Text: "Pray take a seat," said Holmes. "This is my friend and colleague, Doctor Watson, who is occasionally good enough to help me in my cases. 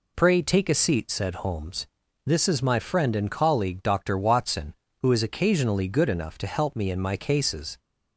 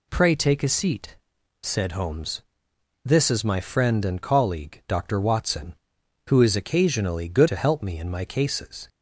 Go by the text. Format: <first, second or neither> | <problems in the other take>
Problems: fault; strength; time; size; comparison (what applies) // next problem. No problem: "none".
first | skips "enough"; at 7.4 s